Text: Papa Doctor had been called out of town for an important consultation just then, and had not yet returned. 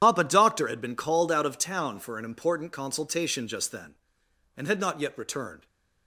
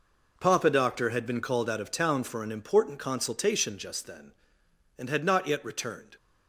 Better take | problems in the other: second | loses the start of "Papa"; at 0.0 s; 60 ms // starts louder than the rest; strong; until 1.0 s; 10 dB

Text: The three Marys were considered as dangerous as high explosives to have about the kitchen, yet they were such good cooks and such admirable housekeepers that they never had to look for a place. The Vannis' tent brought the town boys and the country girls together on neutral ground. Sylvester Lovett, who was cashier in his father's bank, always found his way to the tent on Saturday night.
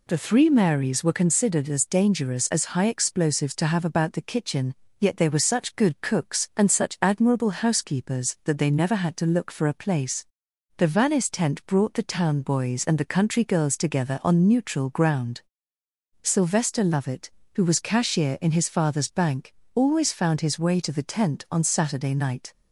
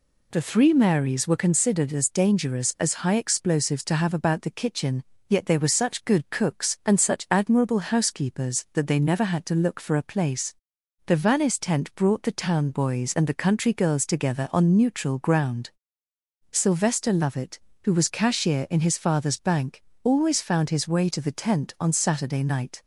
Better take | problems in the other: neither | none

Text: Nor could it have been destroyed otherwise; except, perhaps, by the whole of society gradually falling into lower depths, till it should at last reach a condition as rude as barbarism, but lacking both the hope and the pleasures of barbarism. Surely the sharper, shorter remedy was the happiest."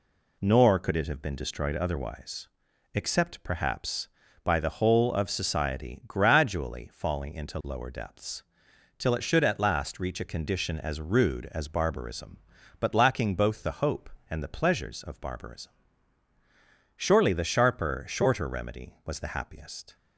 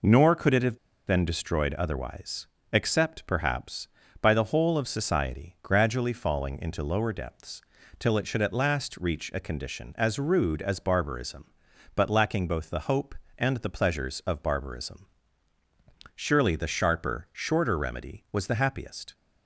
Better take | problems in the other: first | pauses between "have" and "been"; slight; at 0.7 s; 0.29 s long

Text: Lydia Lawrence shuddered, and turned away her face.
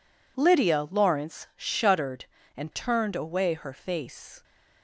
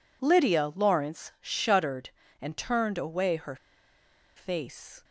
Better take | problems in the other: first | pauses between "her" and "face"; noticeable; at 3.5 s; 0.80 s long

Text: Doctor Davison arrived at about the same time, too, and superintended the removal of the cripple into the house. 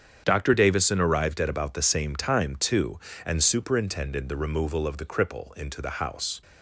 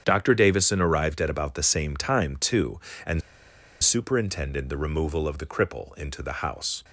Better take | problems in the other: first | starts louder than the rest; strong; until 1.0 s; 8.5 dB; strong in the first // pauses between "and" and "superintended"; noticeable; at 3.2 s; 0.62 s long

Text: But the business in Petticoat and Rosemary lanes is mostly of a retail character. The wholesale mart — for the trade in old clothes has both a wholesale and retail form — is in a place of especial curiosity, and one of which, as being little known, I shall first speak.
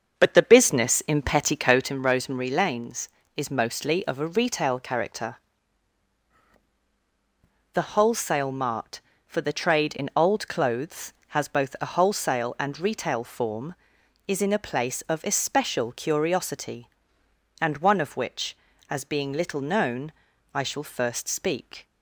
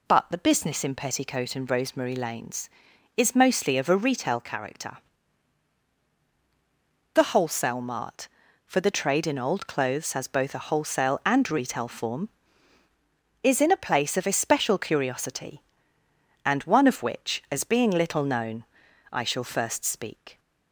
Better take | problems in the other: second | starts louder than the rest; until 2.0 s; 6.5 dB

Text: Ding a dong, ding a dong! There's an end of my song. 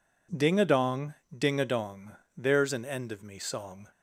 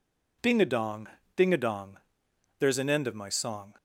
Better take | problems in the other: second | says "me" for "my"; at 3.2 s

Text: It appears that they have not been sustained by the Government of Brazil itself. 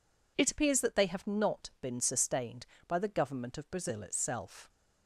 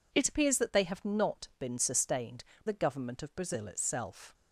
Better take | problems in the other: first | skips "by"; at 2.5 s

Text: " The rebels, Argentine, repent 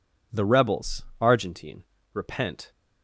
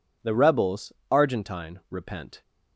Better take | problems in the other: neither | none

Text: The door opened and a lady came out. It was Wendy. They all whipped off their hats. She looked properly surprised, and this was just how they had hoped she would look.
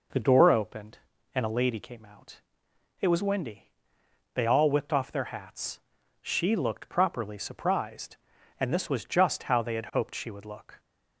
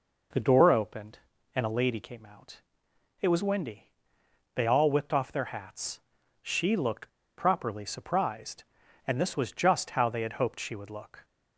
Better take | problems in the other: first | pauses between "looked" and "properly"; slight; at 7.0 s; 0.27 s long

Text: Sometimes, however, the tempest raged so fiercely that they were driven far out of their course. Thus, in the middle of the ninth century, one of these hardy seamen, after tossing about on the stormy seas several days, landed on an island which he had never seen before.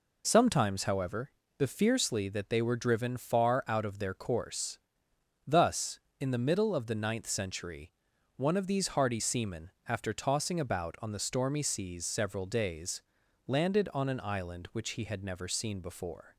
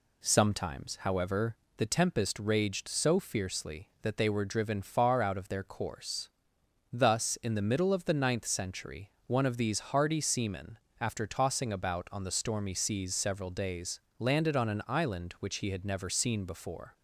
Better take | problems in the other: second | skips "tempest raged so"; at 1.6 s

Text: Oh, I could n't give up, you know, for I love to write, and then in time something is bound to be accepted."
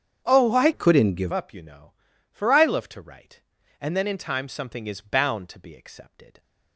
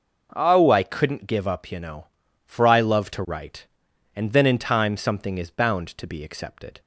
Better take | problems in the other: second | starts louder than the rest; strong; until 1.2 s; 8.5 dB // changes voice from "could" to "give"; from 0.7 to 1.3 s; 0.6 s long

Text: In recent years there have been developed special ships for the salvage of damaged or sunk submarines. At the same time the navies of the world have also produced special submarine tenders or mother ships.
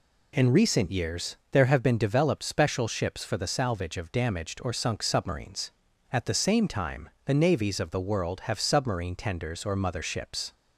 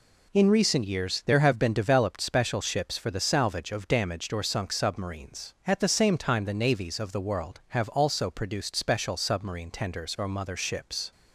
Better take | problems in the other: second | pauses between "years" and "there"; slight; at 1.3 s; 0.16 s long // pauses between "time" and "the"; slight; at 7.0 s; 0.16 s long // skips "also produced special"; at 8.5 s

